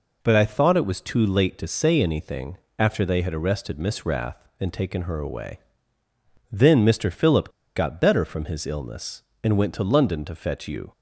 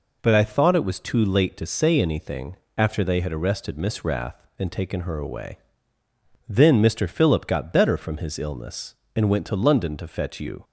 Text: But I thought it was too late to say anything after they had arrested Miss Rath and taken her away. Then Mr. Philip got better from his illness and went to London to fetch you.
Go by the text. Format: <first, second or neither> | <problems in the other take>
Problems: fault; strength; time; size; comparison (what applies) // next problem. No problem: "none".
second | pauses between "anything" and "after"; slight; at 2.5 s; 0.20 s long; slight in the second // pauses between "Philip" and "got"; slight; at 7.4 s; 0.27 s long